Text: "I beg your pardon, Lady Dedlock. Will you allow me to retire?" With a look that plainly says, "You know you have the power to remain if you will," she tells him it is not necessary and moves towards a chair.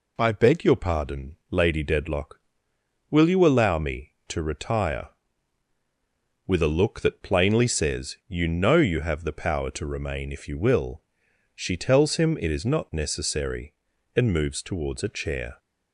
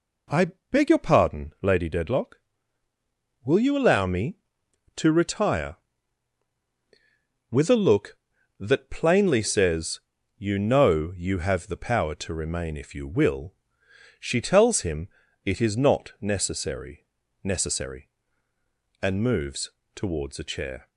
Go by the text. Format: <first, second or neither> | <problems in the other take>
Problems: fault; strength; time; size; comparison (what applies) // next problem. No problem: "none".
first | pauses between "I" and "beg"; slight; at 0.5 s; 0.20 s long // pauses between "him" and "it"; at 15.0 s; 0.38 s long // says "necessary" twice; at 17.4 s // pauses between "moves" and "towards"; slight; at 19.7 s; 0.24 s long